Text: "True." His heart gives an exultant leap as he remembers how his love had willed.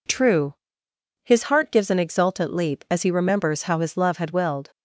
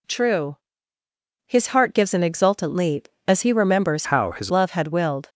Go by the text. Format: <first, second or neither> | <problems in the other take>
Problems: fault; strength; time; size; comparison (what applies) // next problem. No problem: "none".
first | changes voice from "how" to "his"; from 4.0 to 4.5 s; 0.5 s long